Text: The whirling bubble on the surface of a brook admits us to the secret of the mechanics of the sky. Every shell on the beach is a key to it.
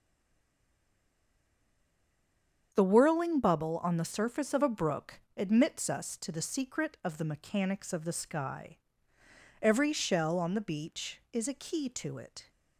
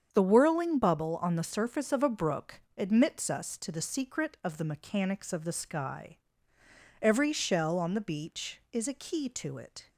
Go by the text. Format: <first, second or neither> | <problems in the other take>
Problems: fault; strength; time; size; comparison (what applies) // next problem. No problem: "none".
second | stays silent before the first word; strong; until 2.7 s; 2.7 s long // starts louder than the rest; strong; until 3.7 s; 7.5 dB; strong in the second // pauses between "brook" and "admits"; slight; at 5.1 s; 0.18 s long; slight in the second